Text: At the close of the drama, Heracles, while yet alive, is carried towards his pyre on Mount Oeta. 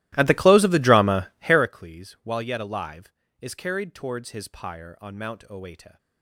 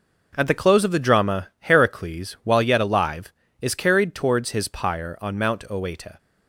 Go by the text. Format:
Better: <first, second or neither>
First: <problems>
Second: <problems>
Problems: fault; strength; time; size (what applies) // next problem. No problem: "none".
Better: second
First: starts louder than the rest; strong; until 1.7 s; 16.5 dB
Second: none